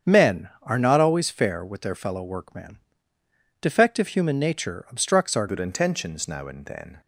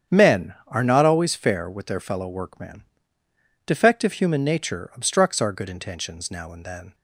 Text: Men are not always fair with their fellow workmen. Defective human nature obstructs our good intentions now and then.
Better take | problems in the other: second | starts louder than the rest; strong; until 1.1 s; 8 dB; strong in the second // changes voice at "good"; from 5.4 s on; 1.6 s long

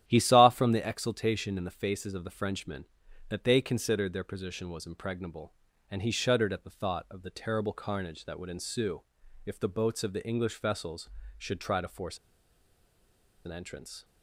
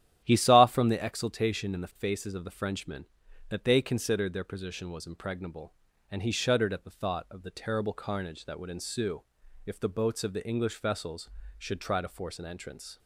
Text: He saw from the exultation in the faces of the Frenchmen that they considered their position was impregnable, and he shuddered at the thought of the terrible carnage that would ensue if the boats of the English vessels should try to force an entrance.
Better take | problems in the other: second | starts louder than the rest; strong; until 1.0 s; 11 dB; strong in the second // pauses between "ensue" and "if"; at 9.0 s; 0.44 s long; also in the second // pauses between "force" and "an"; strong; at 12.1 s; 1.2 s long

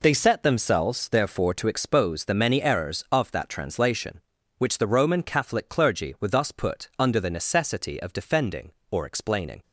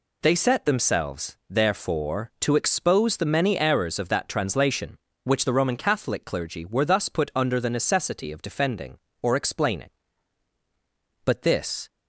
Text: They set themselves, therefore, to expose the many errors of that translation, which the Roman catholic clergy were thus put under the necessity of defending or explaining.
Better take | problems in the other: first | goes on to say "But this"; noticeable; from 11.2 s on; 0.64 s long

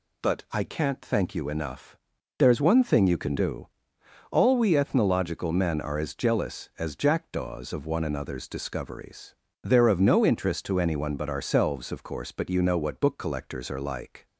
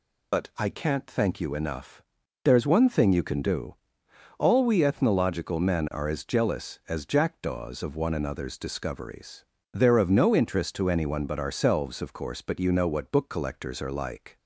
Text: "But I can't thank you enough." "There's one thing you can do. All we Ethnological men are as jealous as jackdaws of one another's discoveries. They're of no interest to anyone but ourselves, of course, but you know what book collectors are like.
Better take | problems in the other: first | loses the start of "But"; at 0.3 s; 40 ms

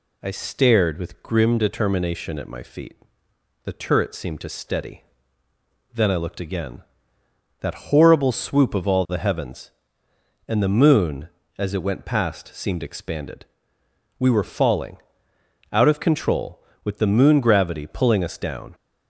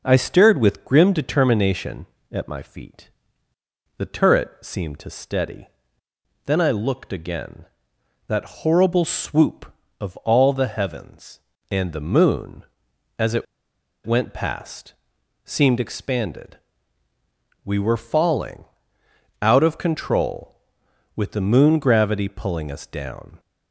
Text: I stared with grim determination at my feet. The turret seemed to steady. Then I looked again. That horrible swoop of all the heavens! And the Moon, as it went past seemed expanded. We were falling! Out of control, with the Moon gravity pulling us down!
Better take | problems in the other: first | pauses between "it" and "went"; noticeable; at 13.4 s; 0.60 s long // pauses between "past" and "seemed"; noticeable; at 14.9 s; 0.50 s long

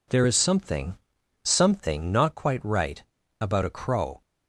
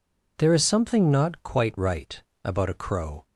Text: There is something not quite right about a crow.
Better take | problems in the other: second | says "something" twice; at 1.4 s // pauses between "right" and "about"; at 3.0 s; 0.38 s long; slight in the second

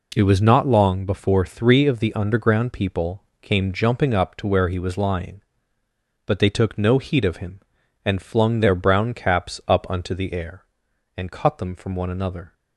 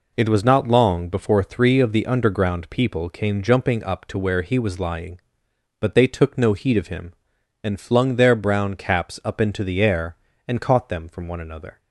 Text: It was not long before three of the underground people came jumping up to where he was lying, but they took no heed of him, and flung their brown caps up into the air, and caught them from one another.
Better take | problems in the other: second | pauses between "people" and "came"; slight; at 3.2 s; 0.18 s long // says "unto" for "into"; at 9.8 s

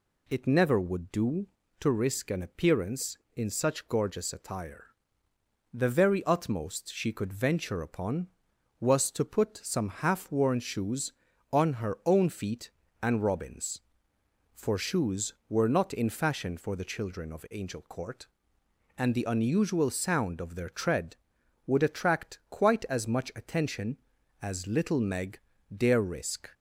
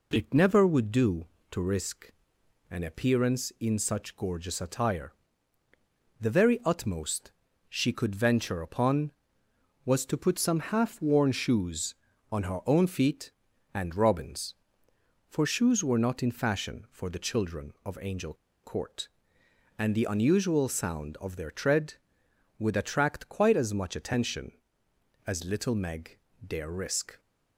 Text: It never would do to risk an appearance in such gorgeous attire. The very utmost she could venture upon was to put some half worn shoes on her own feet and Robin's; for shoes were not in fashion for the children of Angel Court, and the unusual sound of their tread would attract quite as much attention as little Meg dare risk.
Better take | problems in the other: first | pauses between "risk" and "an"; noticeable; at 2.1 s; 0.58 s long // pauses between "utmost" and "she"; at 7.3 s; 0.38 s long // pauses between "Angel" and "Court"; slight; at 18.3 s; 0.29 s long // pauses between "Meg" and "dare"; slight; at 26.1 s; 0.30 s long; slight in the first

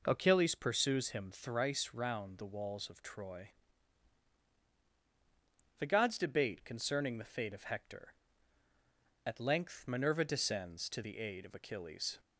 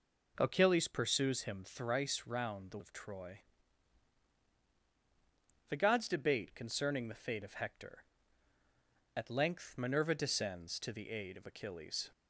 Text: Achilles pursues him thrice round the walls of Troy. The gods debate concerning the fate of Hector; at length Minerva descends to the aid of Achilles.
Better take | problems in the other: first | skips "walls"; at 2.7 s

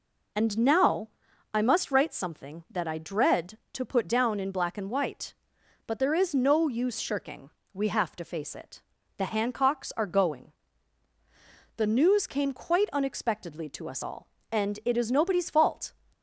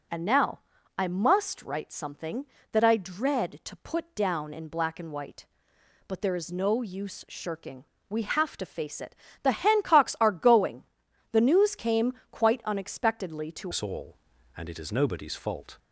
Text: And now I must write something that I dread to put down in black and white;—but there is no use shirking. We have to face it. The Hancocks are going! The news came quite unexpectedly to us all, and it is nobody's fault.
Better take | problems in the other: first | pauses between "now" and "I"; slight; at 0.6 s; 0.36 s long; also in the first // pauses between "came" and "quite"; slight; at 12.1 s; 0.18 s long // changes voice at "us"; from 13.7 s on; 2.0 s long

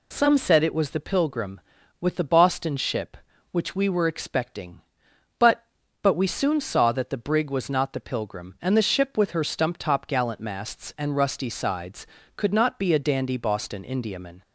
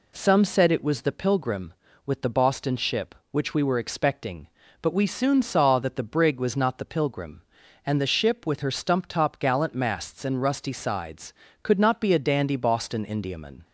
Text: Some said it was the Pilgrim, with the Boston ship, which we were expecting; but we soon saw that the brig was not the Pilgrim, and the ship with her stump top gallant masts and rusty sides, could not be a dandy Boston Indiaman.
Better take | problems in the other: second | says "but" twice; at 6.0 s

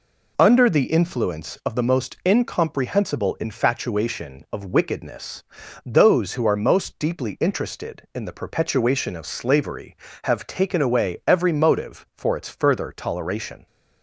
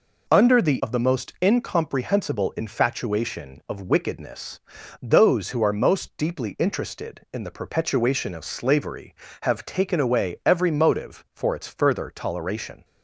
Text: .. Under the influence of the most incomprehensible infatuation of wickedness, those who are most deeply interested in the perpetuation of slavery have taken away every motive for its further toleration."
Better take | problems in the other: first | skips "influence"; at 0.8 s

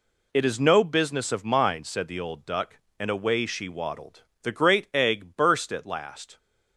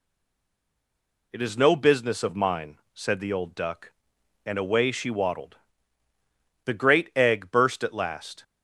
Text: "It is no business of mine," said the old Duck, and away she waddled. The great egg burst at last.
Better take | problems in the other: first | stays silent before the first word; noticeable; until 1.3 s; 1.3 s long

